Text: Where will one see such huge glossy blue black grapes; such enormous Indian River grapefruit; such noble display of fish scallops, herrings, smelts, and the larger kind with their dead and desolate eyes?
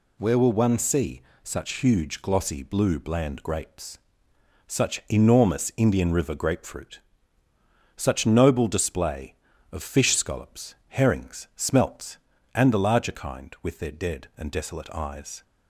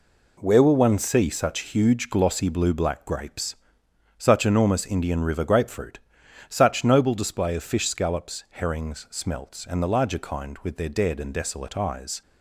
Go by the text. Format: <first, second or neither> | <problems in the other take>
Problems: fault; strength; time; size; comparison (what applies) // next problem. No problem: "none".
second | pauses between "see" and "such"; slight; at 1.2 s; 0.24 s long // says "bland" for "black"; at 2.9 s